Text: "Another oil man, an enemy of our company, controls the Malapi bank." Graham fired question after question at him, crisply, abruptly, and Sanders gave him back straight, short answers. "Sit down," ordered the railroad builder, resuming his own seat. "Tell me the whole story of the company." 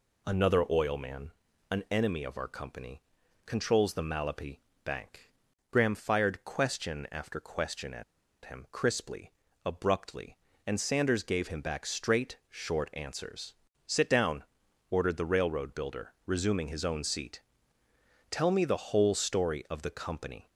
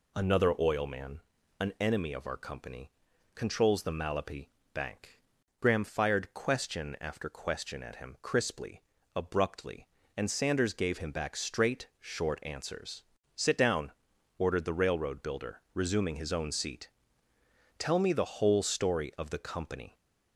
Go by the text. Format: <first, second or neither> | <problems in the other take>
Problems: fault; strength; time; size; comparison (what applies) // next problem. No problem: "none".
second | pauses between "Malapi" and "bank"; slight; at 4.6 s; 0.24 s long; slight in the second // pauses between "at" and "him"; at 8.0 s; 0.41 s long